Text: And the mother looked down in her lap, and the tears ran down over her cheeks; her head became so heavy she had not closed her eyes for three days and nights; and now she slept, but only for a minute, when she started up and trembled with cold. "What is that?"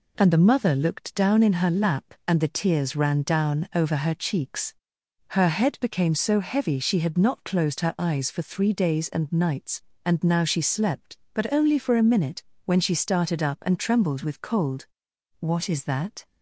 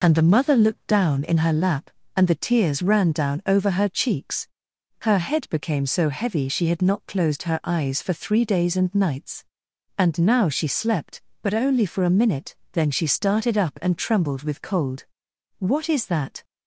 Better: first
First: none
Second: says "then" for "when"; at 12.7 s

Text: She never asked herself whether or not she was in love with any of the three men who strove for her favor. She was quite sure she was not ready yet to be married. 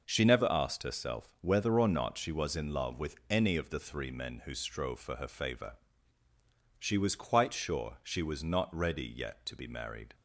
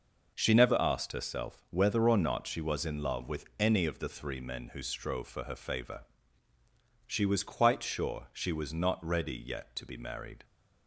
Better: neither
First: pauses between "with" and "any"; slight; at 3.1 s; 0.16 s long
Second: pauses between "with" and "any"; slight; at 3.4 s; 0.16 s long

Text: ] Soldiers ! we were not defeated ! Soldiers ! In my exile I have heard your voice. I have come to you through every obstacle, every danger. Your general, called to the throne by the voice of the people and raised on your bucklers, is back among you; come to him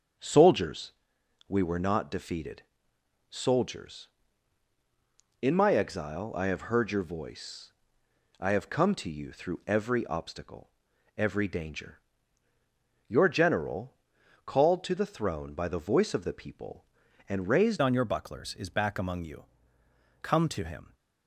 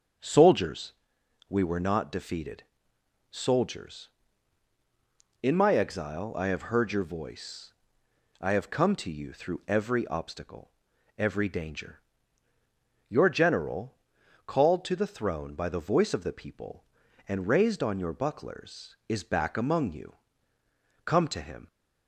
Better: second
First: starts louder than the rest; strong; until 1.7 s; 7.5 dB // changes voice at "on"; from 17.8 s on; 3.1 s long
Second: starts louder than the rest; strong; until 1.7 s; 7.5 dB

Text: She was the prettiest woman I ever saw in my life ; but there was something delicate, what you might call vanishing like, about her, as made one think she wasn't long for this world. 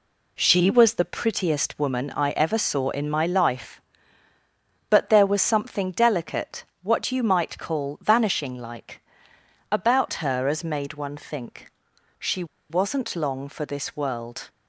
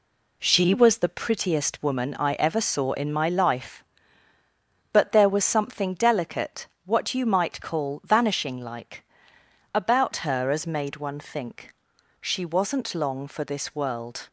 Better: second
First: pauses between "think" and "she"; noticeable; at 11.7 s; 0.46 s long // pauses between "she" and "wasn't"; slight; at 12.4 s; 0.25 s long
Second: pauses between "think" and "she"; at 11.7 s; 0.44 s long

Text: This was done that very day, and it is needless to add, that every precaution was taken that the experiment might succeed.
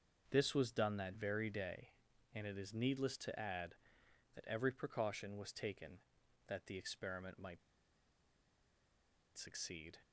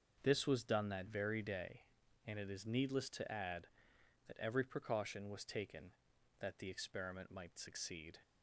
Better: second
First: starts louder than the rest; until 1.3 s; 6.5 dB // pauses between "might" and "succeed"; strong; at 7.6 s; 1.7 s long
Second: starts louder than the rest; until 1.2 s; 6.5 dB

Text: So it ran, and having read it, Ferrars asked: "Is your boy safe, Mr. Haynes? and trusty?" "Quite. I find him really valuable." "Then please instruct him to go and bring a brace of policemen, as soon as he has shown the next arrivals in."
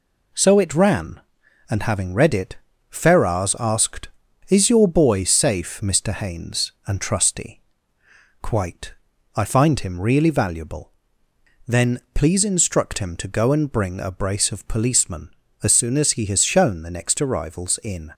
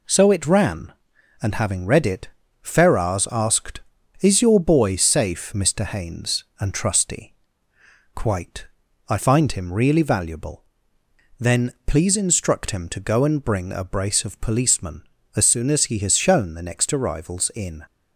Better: neither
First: none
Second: none

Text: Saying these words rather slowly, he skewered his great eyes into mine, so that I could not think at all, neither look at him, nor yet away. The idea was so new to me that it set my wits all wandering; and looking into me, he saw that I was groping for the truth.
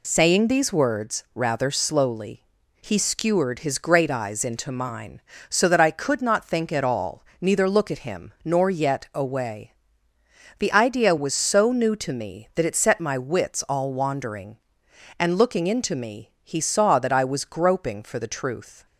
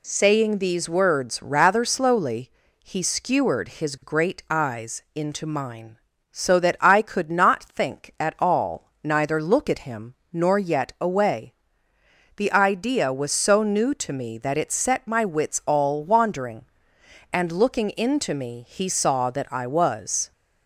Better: first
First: none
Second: stops before "groping for the truth"; at 20.3 s

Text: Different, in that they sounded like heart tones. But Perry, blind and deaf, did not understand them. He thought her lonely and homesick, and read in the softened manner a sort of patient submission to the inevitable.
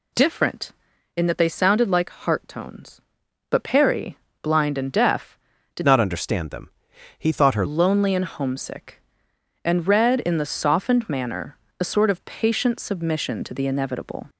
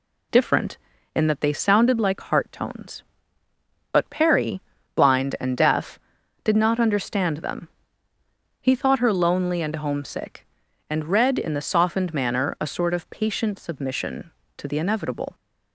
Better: second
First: changes voice from "not" to "her"; from 5.8 to 7.6 s; 1.8 s long // pauses between "manner" and "a"; slight; at 11.5 s; 0.22 s long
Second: none

